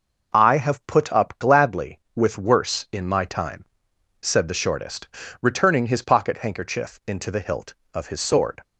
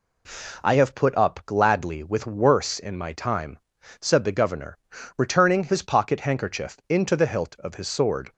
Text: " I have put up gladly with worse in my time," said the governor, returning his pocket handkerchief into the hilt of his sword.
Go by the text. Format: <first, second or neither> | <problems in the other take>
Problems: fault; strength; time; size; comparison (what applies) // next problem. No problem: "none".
second | says "shortest" for "governor"; at 4.5 s